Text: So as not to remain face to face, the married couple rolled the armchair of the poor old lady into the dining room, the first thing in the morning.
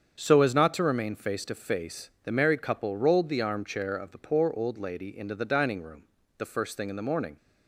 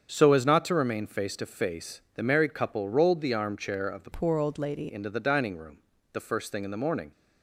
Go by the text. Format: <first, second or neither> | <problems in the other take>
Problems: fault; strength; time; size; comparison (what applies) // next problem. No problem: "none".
first | starts louder than the rest; strong; until 1.1 s; 7.5 dB; strong in the first // changes voice from "poor" to "lady"; from 4.1 to 4.8 s; 0.7 s long